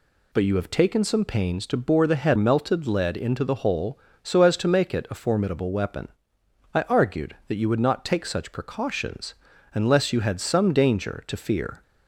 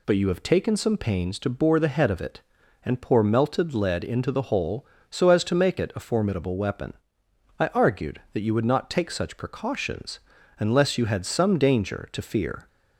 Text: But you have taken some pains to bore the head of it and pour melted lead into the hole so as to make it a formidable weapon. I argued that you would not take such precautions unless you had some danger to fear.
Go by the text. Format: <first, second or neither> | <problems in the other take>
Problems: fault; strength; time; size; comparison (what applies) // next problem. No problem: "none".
second | skips "of it and pour"; at 2.3 s // pauses between "precautions" and "unless"; at 9.3 s; 0.40 s long; also in the second